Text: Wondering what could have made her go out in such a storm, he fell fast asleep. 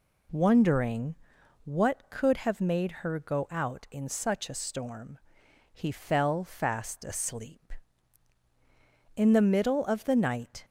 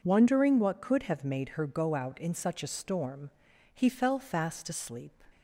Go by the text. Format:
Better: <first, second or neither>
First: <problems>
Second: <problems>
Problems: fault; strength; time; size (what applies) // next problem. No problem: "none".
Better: second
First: pauses between "Wondering" and "what"; noticeable; at 1.1 s; 0.48 s long // goes on to say "In the middle of the night"; from 9.1 s on; 1.4 s long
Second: none